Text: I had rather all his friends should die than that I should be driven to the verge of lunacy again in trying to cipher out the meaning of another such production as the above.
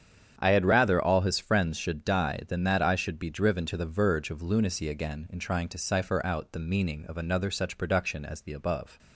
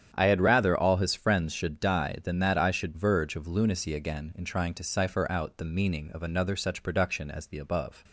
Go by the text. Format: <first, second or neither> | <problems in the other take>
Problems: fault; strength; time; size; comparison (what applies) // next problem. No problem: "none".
first | starts louder than the rest; strong; until 1.1 s; 9 dB; strong in the first // skips "be driven to the"; at 2.9 s